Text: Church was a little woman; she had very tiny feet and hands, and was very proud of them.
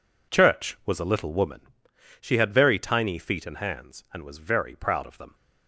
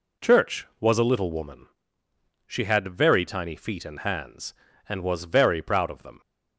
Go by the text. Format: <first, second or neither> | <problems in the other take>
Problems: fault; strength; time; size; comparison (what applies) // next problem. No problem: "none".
neither | none